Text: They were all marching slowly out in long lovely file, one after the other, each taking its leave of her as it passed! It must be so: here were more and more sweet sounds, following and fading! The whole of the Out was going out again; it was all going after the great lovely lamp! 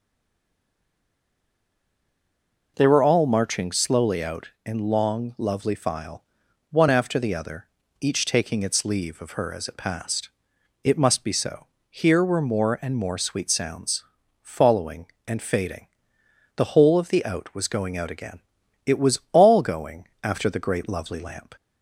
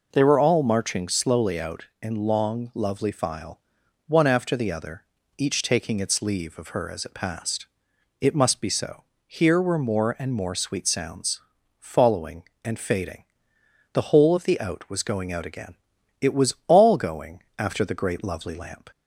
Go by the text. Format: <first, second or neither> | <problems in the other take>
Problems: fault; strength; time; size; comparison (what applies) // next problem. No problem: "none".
second | stays silent before the first word; strong; until 2.7 s; 2.7 s long